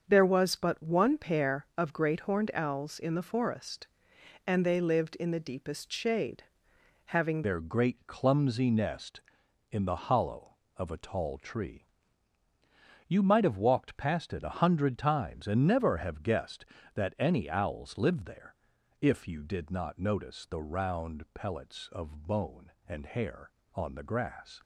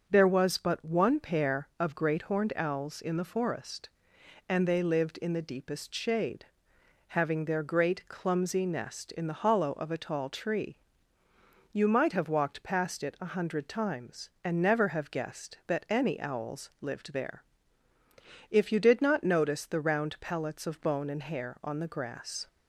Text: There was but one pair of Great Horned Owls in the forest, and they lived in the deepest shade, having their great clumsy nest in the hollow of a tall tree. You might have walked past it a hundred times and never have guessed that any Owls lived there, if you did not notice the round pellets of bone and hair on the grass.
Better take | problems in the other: second | starts louder than the rest; until 1.0 s; 6.5 dB; also in the second // changes voice at "their"; from 7.4 s on; 17.2 s long

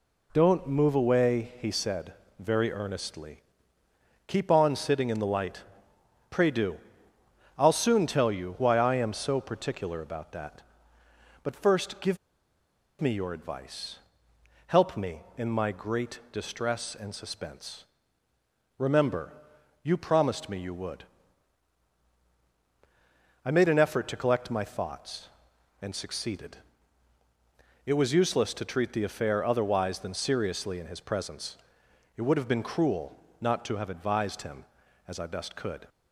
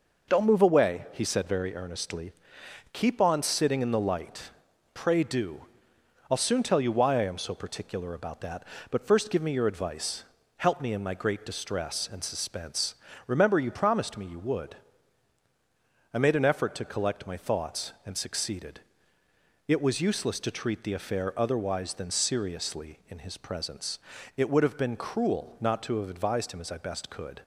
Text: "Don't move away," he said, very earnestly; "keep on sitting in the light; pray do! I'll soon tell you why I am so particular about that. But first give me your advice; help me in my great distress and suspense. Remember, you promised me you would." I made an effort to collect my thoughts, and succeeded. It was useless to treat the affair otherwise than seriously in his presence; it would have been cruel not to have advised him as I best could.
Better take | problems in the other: second | pauses between "give" and "me"; noticeable; at 12.1 s; 0.83 s long // pauses between "cruel" and "not"; slight; at 33.1 s; 0.22 s long

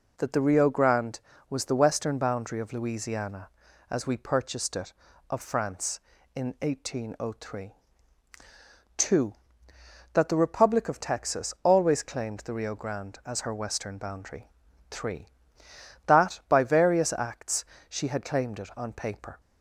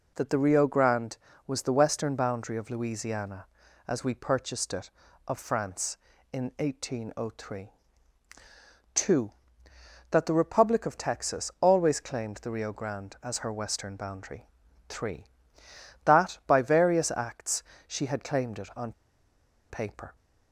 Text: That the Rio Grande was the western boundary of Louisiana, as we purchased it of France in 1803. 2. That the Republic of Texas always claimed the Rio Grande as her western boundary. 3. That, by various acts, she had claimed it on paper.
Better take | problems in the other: first | pauses between "on" and "paper"; noticeable; at 18.9 s; 0.78 s long

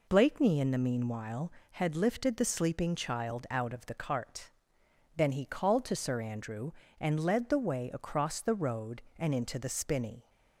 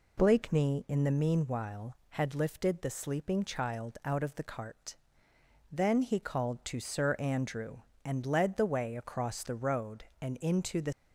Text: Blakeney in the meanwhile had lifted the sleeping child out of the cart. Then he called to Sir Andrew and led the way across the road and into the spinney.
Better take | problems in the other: first | stops before "spinney"; at 10.9 s

